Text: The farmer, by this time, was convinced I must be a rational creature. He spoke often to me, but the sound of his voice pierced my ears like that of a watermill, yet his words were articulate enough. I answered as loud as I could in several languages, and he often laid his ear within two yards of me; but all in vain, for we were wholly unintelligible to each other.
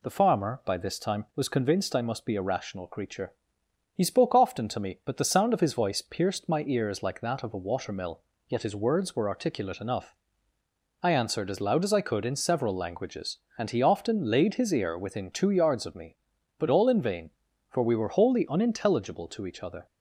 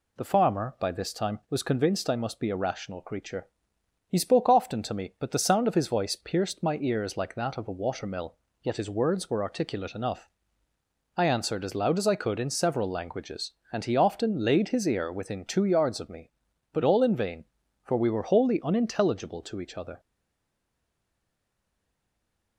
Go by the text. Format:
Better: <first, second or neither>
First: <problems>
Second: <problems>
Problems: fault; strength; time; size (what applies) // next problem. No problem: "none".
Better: first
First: none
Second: stays silent after the last word; strong; from 19.9 s on; 2.6 s long